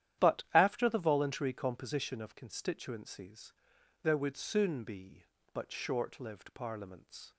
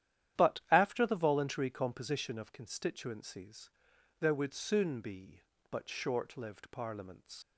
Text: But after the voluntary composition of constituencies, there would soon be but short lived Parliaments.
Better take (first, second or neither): first